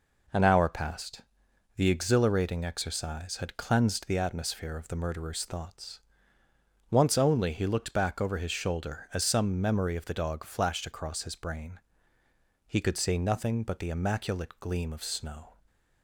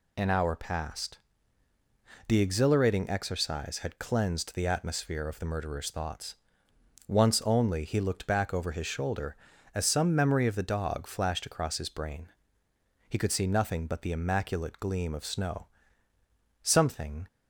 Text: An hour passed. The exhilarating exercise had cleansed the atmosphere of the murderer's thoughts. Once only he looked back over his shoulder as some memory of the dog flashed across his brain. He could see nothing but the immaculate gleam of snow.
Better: first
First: none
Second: goes on to say "Something"; noticeable; from 16.6 s on; 0.64 s long

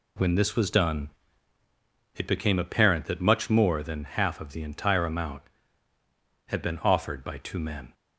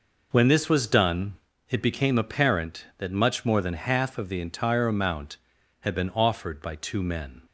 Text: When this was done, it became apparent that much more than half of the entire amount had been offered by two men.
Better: neither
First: none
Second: none

